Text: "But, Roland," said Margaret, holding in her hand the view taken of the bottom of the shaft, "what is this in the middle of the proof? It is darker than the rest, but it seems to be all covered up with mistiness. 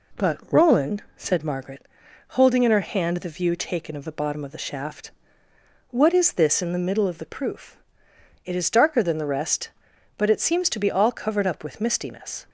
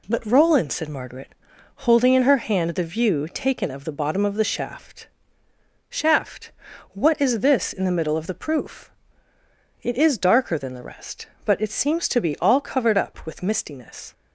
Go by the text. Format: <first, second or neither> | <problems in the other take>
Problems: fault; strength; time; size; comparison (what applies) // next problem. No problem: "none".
first | says "shaft" twice; at 5.8 s